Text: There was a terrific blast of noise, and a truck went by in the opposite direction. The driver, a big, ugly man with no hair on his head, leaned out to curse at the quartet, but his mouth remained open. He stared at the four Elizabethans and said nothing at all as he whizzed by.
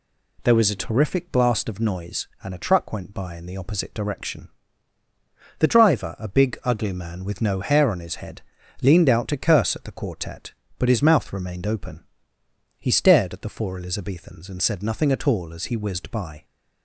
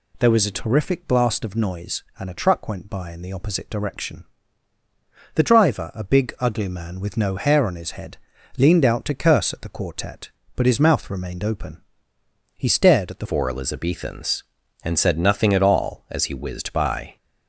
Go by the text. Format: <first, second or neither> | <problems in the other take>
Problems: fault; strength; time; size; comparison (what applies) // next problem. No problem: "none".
first | changes voice at "four"; from 13.2 s on; 3.9 s long